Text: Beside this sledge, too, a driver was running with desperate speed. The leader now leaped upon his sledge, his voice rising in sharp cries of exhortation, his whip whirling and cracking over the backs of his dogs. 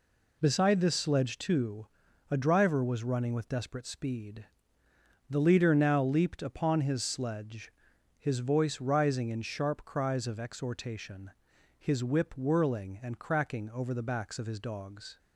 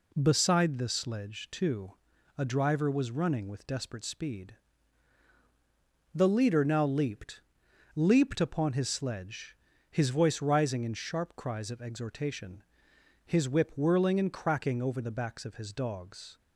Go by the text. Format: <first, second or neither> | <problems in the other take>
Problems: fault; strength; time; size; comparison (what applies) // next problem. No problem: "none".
first | says "leaped" twice; at 7.9 s